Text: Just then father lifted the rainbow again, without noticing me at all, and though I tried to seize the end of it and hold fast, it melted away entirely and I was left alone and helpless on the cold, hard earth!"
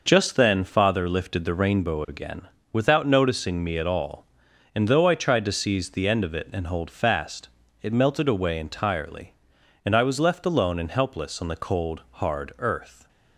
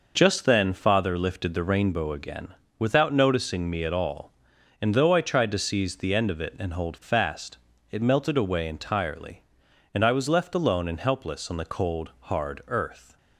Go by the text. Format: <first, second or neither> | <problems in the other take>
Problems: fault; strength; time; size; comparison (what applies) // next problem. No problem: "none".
neither | none